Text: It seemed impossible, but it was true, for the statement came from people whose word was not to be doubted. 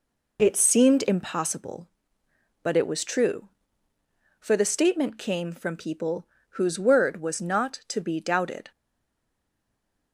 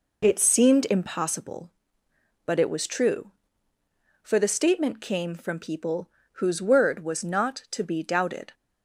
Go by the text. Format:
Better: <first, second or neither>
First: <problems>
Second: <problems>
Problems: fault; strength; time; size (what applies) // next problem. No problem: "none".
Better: second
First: pauses between "people" and "whose"; slight; at 6.2 s; 0.32 s long // stays silent after the last word; noticeable; from 8.7 s on; 1.4 s long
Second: pauses between "people" and "whose"; slight; at 6.0 s; 0.32 s long